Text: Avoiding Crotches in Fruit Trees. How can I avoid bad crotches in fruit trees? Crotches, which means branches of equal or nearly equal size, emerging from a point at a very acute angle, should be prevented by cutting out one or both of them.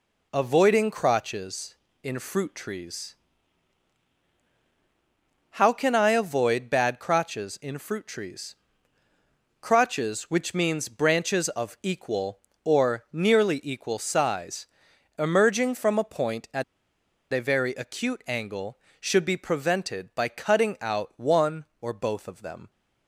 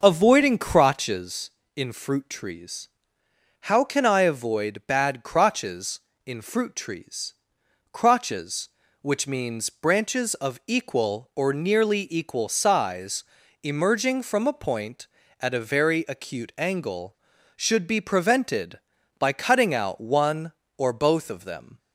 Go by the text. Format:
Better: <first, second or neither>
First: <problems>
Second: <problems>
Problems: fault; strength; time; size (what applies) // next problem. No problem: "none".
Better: second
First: pauses between "at" and "a"; noticeable; at 16.6 s; 0.70 s long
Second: none